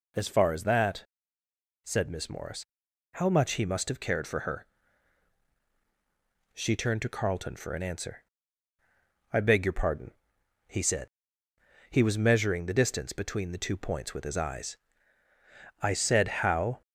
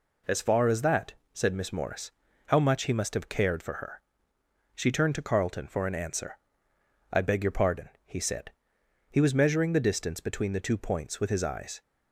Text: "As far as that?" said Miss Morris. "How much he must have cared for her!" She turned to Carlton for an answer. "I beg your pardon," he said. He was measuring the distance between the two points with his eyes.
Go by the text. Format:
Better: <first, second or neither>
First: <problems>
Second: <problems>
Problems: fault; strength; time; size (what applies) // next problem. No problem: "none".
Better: second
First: goes on to say "I said how"; noticeable; from 15.8 s on; 1.0 s long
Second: none